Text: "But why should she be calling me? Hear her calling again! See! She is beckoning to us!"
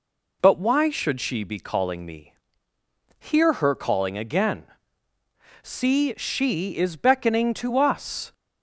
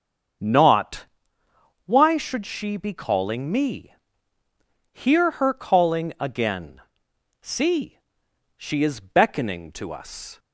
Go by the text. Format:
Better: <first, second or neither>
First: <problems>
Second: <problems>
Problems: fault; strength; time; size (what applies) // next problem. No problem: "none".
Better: first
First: none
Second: starts louder than the rest; until 2.1 s; 7 dB // says "Not" for "But"; at 0.4 s